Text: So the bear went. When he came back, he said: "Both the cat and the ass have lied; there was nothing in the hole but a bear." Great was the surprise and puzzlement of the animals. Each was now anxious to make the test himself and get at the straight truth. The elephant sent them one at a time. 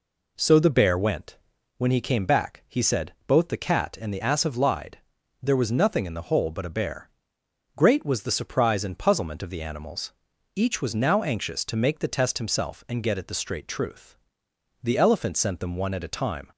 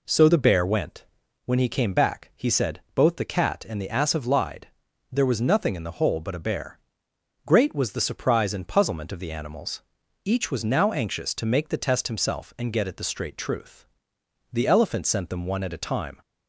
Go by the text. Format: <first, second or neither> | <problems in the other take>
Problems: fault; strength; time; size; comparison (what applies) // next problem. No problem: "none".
neither | none